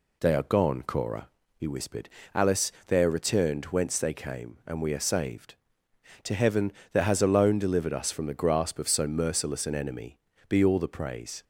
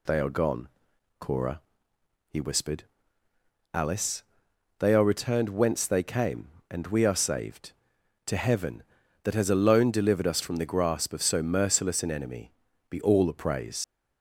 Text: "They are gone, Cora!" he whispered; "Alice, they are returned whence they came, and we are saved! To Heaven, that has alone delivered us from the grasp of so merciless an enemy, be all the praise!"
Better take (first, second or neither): first